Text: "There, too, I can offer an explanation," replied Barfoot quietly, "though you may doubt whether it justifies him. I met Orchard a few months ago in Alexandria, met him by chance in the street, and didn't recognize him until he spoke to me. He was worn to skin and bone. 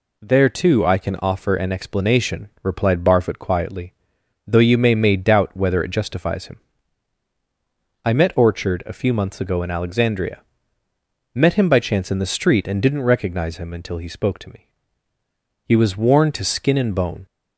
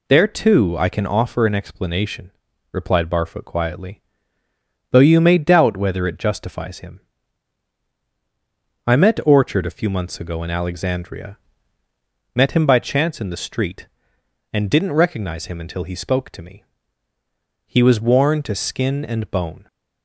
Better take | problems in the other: second | says "may" twice; at 4.9 s

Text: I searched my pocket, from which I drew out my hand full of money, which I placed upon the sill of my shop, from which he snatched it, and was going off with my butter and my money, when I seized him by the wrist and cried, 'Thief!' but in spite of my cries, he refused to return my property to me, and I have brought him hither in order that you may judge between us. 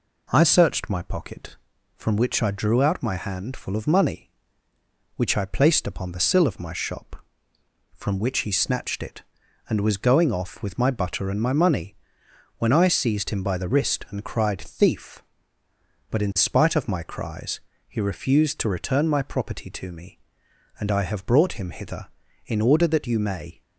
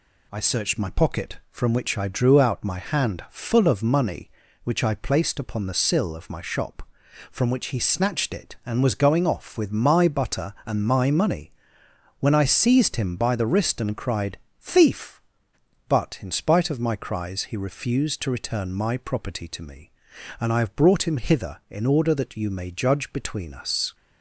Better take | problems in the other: second | stops before "judge between us"; at 23.6 s

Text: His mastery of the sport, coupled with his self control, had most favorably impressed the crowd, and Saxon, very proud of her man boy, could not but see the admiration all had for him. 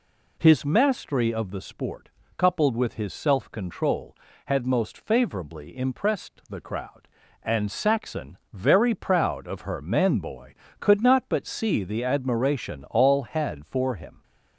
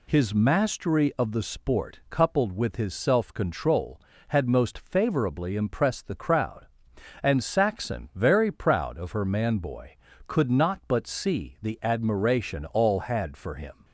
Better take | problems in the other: neither | none

